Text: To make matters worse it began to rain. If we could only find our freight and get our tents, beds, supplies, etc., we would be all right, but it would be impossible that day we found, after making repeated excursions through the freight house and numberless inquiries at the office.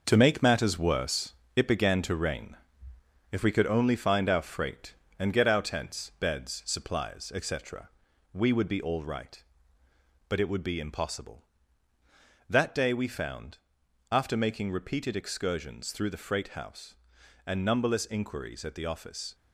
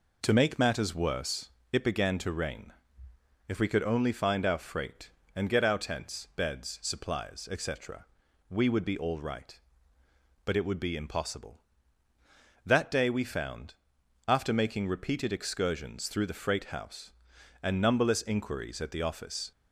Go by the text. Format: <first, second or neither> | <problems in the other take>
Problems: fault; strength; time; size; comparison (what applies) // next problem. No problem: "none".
second | gets quieter; strong; throughout; 7.5 dB // pauses between "worse" and "it"; slight; at 1.3 s; 0.24 s long; slight in the second